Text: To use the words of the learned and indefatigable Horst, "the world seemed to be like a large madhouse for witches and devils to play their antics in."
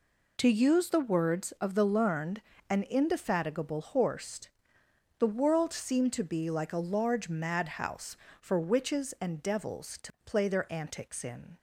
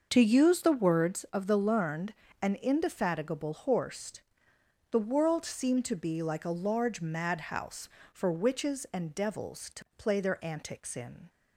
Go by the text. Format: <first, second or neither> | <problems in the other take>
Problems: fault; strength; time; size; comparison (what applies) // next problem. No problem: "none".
first | starts louder than the rest; noticeable; until 1.3 s; 6 dB